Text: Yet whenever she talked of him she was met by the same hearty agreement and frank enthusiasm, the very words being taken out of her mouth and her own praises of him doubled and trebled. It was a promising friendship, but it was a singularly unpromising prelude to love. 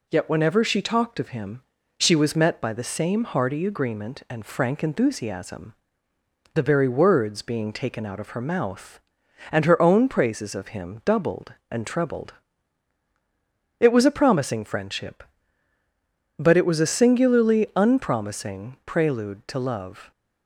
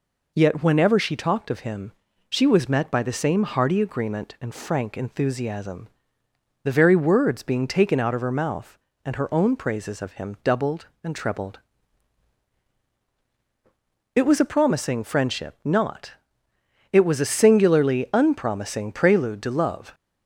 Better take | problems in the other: first | pauses between "him" and "she"; at 1.9 s; 0.38 s long; also in the first // says "not" for "but"; at 15.6 s

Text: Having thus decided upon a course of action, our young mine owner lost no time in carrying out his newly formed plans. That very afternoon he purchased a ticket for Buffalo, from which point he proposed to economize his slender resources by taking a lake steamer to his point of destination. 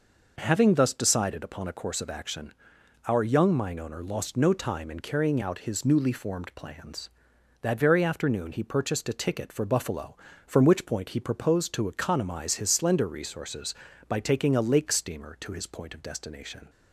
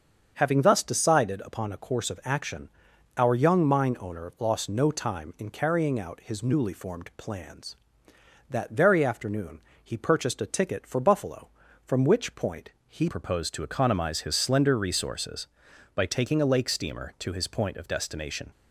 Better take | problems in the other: first | starts louder than the rest; until 1.3 s; 7 dB // pauses between "afternoon" and "he"; slight; at 9.6 s; 0.22 s long // pauses between "point" and "he"; slight; at 12.7 s; 0.18 s long // changes voice at "proposed"; from 13.0 s on; 5.5 s long

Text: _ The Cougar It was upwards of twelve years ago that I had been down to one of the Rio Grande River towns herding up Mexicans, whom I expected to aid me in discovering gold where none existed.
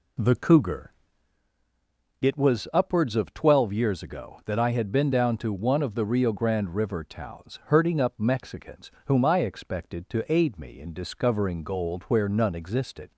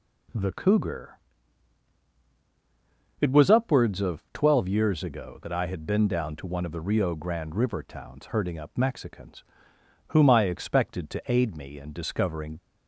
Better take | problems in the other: first | pauses between "Cougar" and "It"; strong; at 1.1 s; 2.0 s long; strong in the first // stops before "gold where none existed"; at 12.5 s

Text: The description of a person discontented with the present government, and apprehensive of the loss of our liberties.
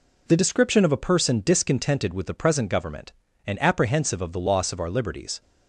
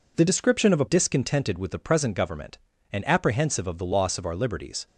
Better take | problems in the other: first | skips "person"; at 0.8 s

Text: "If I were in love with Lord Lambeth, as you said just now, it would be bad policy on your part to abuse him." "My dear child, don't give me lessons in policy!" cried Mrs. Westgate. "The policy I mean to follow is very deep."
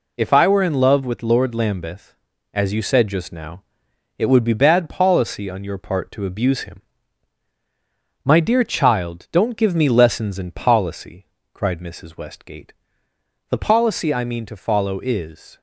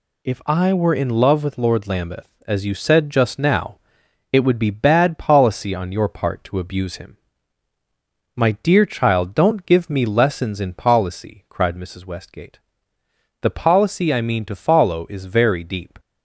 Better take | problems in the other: second | stops before "very deep"; at 15.5 s

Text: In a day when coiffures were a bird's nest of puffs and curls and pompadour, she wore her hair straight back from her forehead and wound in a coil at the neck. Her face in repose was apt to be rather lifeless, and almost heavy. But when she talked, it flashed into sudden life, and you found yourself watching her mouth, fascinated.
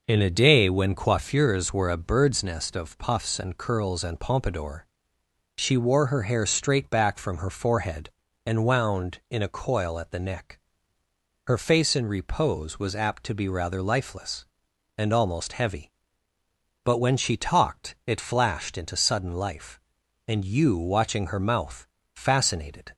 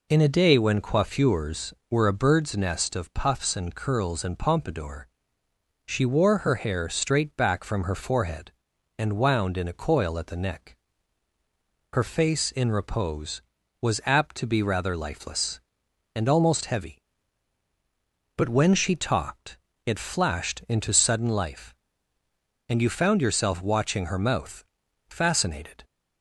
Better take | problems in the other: second | skips "found yourself"; at 20.7 s

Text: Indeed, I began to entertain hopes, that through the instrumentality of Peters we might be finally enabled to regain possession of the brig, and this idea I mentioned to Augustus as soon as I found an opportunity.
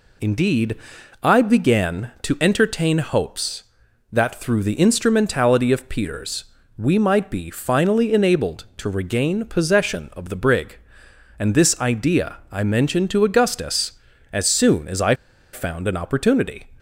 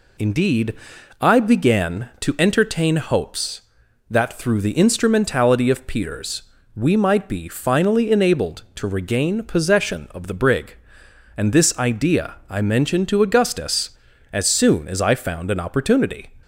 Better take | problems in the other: second | pauses between "Peters" and "we"; slight; at 6.4 s; 0.34 s long; slight in the second // pauses between "I" and "found"; at 15.1 s; 0.39 s long

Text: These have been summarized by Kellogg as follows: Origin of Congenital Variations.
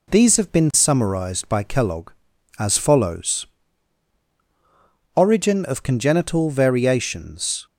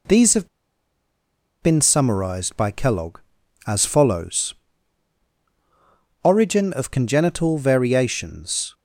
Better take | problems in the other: first | pauses between "have" and "been"; at 0.4 s; 1.1 s long

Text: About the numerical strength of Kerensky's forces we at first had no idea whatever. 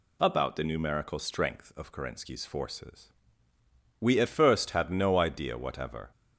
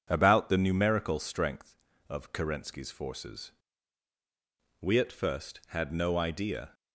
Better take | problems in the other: first | pauses between "forces" and "we"; strong; at 3.5 s; 1.2 s long; noticeable in the first // stops before "whatever"; at 6.7 s

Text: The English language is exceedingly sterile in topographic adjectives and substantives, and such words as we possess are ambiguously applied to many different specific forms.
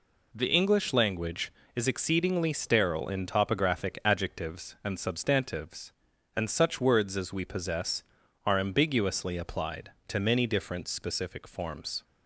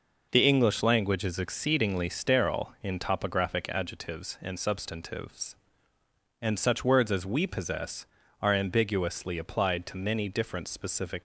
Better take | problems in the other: first | stops before "forms"; at 11.1 s

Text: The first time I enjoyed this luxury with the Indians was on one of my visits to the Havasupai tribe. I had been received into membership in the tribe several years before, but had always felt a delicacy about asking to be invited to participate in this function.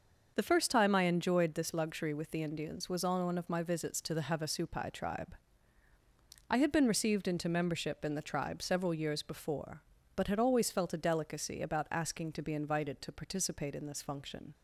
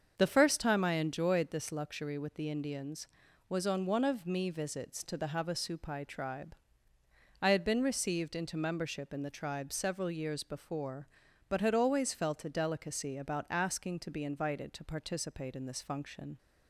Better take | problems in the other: first | starts louder than the rest; until 1.1 s; 7 dB; noticeable in the first // says "me" for "my"; at 4.2 s

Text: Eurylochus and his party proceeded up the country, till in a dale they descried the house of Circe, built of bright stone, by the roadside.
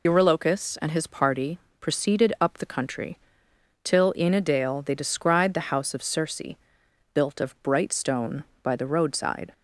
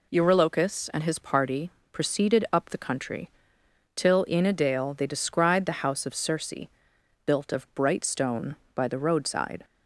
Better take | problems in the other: second | loses the start of "Eurylochus"; at 0.0 s; 65 ms // pauses between "party" and "proceeded"; slight; at 1.5 s; 0.22 s long; slight in the second

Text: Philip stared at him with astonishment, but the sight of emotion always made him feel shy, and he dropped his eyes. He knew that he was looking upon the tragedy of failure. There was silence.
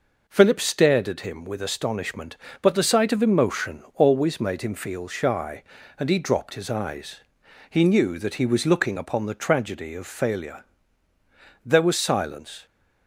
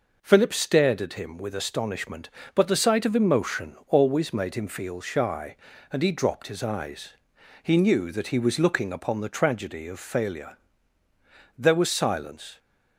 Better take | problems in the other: neither | none

